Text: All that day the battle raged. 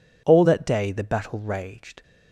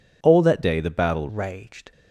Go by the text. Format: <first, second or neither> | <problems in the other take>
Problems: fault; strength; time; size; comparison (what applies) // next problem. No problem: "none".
first | changes voice from "day" to "battle"; from 0.6 to 1.2 s; 0.6 s long